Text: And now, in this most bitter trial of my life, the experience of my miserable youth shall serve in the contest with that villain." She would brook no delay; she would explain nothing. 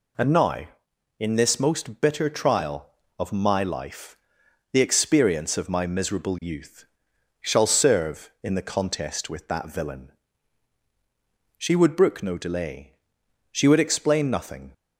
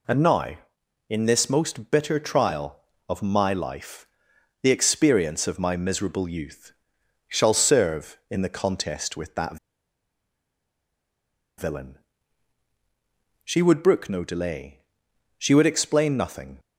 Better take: first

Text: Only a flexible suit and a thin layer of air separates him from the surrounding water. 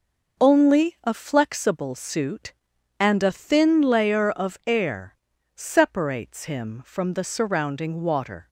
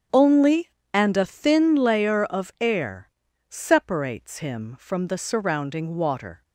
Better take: first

